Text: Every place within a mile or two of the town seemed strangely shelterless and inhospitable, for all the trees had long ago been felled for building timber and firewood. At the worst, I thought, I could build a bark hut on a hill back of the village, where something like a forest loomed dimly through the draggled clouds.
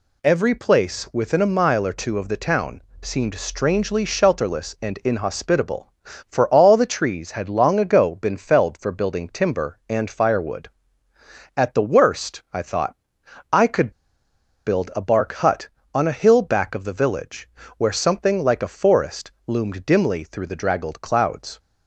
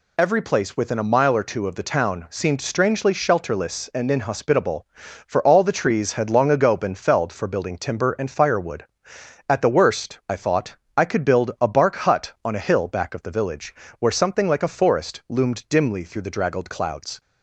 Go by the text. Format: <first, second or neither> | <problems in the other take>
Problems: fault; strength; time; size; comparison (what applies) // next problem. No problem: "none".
second | pauses between "town" and "seemed"; slight; at 2.8 s; 0.20 s long // pauses between "could" and "build"; noticeable; at 13.9 s; 0.75 s long // pauses between "forest" and "loomed"; slight; at 19.3 s; 0.16 s long